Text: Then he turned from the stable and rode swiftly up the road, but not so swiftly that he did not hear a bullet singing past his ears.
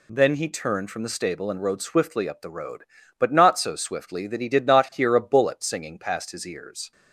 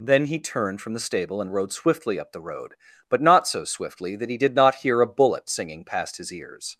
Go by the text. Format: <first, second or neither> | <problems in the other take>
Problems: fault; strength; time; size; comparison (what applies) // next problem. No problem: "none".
neither | none